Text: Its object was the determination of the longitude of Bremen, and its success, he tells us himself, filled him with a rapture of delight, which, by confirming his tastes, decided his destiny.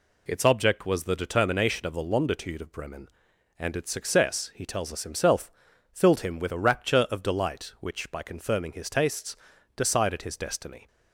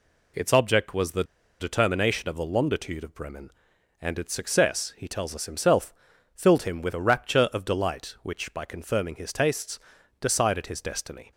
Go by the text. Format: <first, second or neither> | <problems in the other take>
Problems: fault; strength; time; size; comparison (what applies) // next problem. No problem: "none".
first | pauses between "the" and "determination"; at 1.2 s; 0.37 s long